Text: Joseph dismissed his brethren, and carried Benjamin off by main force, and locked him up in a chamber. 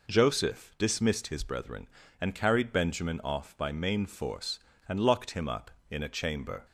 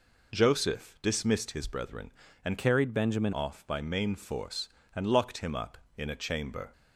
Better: first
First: none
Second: changes voice from "carried" to "Benjamin"; from 2.5 to 3.3 s; 0.8 s long

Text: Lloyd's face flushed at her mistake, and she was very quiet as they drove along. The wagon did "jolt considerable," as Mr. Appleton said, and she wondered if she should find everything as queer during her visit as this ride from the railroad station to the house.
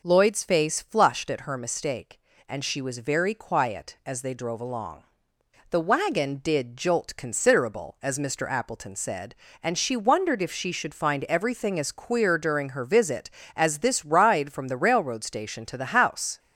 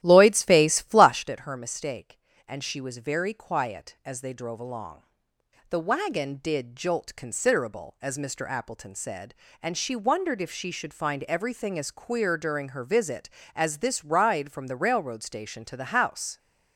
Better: first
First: none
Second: starts louder than the rest; strong; until 1.3 s; 13.5 dB

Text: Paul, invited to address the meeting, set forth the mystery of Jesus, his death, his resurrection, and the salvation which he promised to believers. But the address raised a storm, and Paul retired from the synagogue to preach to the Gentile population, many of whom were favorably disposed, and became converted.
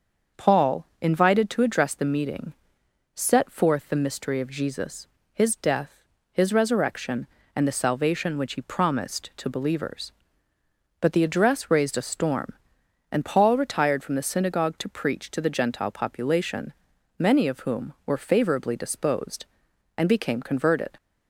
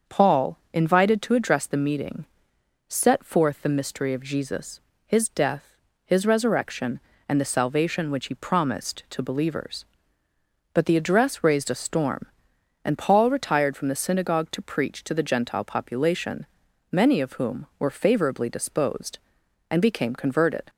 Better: neither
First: starts louder than the rest; until 1.5 s; 6.5 dB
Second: starts louder than the rest; until 1.2 s; 6.5 dB

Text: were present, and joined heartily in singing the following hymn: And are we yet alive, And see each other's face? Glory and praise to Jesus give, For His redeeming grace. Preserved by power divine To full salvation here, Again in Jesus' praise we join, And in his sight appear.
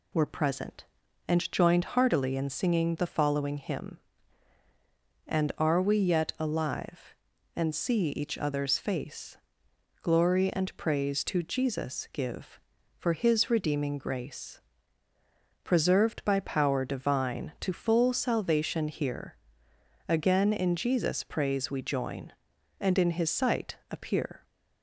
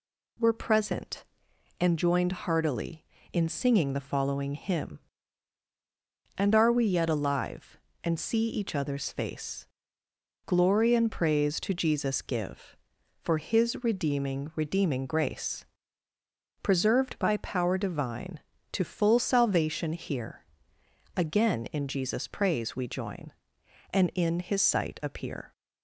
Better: first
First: none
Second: says "redeeming" twice; at 14.5 s

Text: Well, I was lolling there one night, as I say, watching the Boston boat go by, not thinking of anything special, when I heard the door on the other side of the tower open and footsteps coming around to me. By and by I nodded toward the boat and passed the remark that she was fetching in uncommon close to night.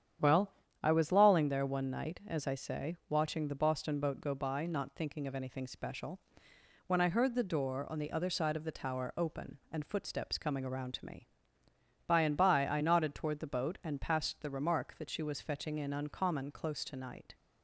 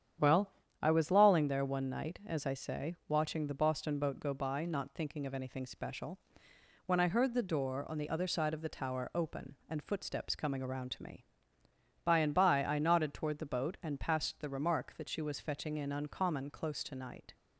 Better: neither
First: starts louder than the rest; strong; until 1.5 s; 9 dB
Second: starts louder than the rest; strong; until 1.5 s; 9 dB

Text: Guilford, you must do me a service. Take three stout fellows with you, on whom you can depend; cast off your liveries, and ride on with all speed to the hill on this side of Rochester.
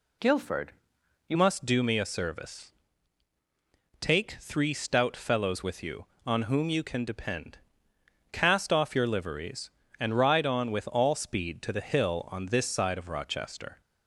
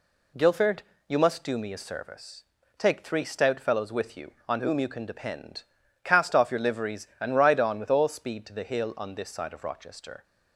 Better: second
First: changes voice at "must"; from 1.3 s on; 12.5 s long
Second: none

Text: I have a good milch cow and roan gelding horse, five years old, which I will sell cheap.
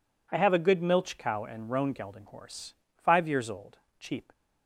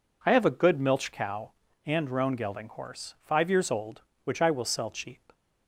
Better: second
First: skips "which I will sell"; at 3.8 s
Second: none

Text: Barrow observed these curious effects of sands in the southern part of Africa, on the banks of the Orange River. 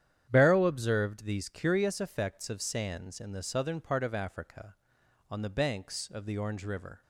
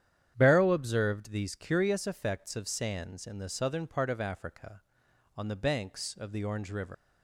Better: first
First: starts louder than the rest; strong; until 1.3 s; 10 dB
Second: starts louder than the rest; strong; until 1.3 s; 9.5 dB // leaves "River" unfinished; at 6.9 s; 135 ms

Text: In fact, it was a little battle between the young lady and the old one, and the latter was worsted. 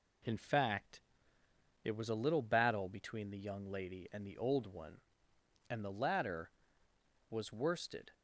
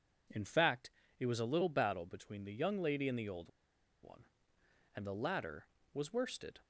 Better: first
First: none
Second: pauses between "old" and "one"; noticeable; at 3.4 s; 0.55 s long

